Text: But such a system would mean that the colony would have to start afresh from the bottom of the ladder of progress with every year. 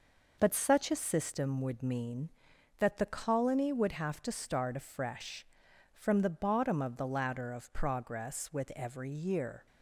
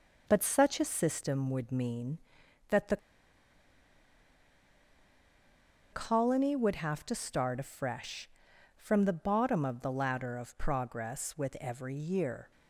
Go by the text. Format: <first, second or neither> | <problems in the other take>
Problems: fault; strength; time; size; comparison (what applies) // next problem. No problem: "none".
first | pauses between "the" and "colony"; strong; at 2.9 s; 2.9 s long